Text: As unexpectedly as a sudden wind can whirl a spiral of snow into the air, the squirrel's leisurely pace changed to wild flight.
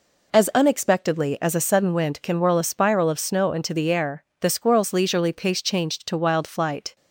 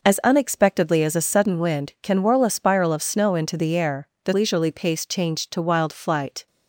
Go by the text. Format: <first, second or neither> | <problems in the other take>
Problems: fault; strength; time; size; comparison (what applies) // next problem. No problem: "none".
first | skips "squirrel's"; at 4.3 s